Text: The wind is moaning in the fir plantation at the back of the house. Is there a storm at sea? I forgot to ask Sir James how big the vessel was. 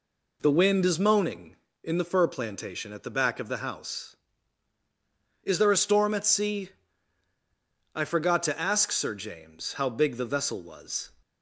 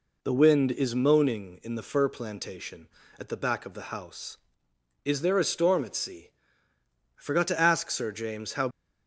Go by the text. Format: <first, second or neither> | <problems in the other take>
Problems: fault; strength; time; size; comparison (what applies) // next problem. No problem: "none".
first | stops before "big the vessel was"; at 8.7 s